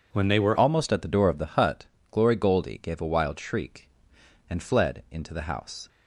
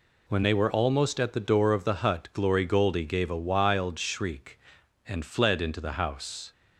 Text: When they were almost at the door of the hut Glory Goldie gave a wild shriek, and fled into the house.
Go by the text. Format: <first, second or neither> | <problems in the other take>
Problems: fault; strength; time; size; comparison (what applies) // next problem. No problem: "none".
second | changes voice at "almost"; from 0.5 s on; 5.3 s long // pauses between "hut" and "Glory"; slight; at 1.8 s; 0.24 s long